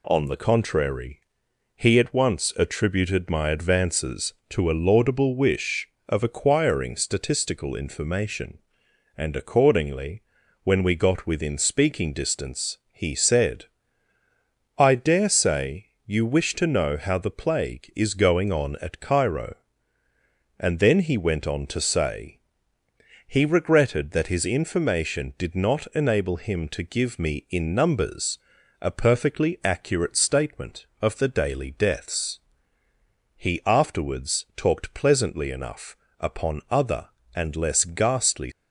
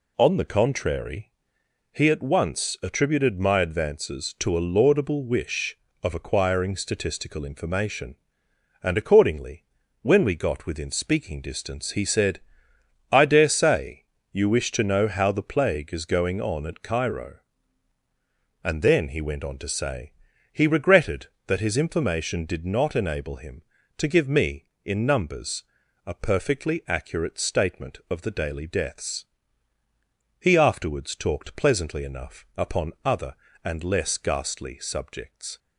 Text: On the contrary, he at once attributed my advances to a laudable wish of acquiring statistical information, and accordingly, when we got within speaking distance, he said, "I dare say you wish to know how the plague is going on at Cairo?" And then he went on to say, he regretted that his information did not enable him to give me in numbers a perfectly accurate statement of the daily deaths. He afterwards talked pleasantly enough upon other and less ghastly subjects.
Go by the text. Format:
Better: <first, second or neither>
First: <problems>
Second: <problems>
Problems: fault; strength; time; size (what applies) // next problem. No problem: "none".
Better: second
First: pauses between "say" and "you"; slight; at 15.8 s; 0.18 s long // pauses between "numbers" and "a"; at 28.3 s; 0.42 s long // pauses between "enough" and "upon"; slight; at 35.9 s; 0.24 s long // stops before "subjects"; at 38.5 s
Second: pauses between "say" and "you"; slight; at 14.0 s; 0.26 s long // pauses between "numbers" and "a"; at 25.6 s; 0.42 s long